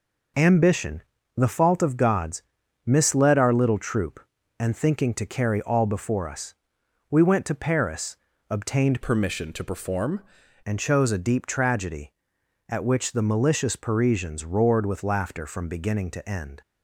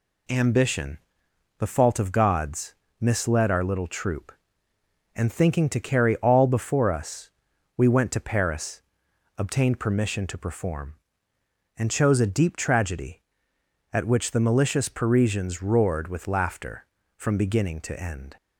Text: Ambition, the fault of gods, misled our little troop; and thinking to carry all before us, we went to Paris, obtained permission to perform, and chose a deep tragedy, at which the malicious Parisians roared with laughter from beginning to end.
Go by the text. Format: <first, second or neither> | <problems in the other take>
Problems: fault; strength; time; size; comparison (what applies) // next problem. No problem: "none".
second | changes voice from "permission" to "perform"; from 9.0 to 10.2 s; 1.2 s long